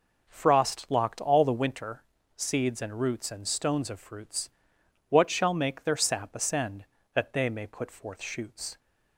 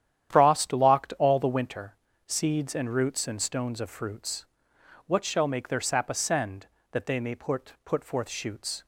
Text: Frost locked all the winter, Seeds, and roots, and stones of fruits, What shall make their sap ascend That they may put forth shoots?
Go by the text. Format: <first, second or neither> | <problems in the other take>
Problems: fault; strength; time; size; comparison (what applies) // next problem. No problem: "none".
first | starts louder than the rest; strong; until 1.4 s; 10 dB // says "put" twice; at 7.8 s